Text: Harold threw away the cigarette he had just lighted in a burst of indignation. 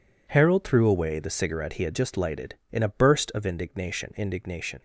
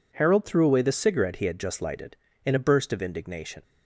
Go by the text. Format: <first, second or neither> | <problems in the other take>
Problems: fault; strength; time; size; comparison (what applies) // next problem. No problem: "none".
second | says "indignation" twice; at 4.1 s